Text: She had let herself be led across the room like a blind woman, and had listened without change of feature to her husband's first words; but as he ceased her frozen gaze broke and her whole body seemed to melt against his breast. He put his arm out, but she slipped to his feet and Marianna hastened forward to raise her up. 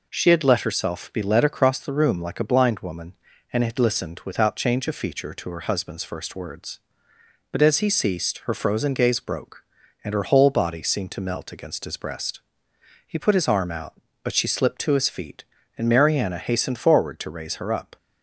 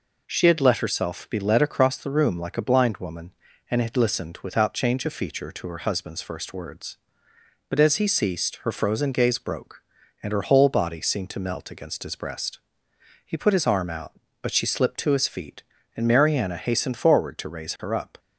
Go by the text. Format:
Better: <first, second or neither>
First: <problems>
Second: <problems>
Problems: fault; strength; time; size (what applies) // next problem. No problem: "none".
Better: neither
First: none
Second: none